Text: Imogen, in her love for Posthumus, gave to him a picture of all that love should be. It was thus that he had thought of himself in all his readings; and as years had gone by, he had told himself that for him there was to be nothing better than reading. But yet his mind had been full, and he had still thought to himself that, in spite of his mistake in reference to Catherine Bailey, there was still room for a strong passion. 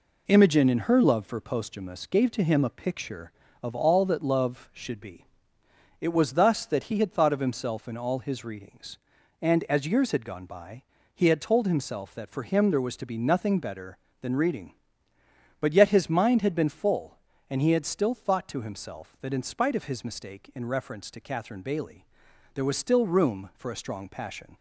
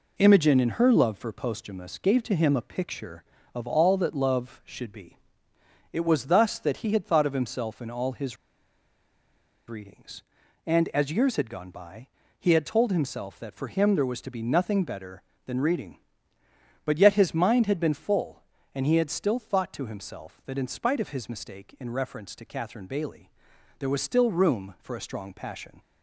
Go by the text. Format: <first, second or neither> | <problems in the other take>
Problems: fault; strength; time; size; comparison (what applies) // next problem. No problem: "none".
first | pauses between "his" and "readings"; strong; at 8.3 s; 1.3 s long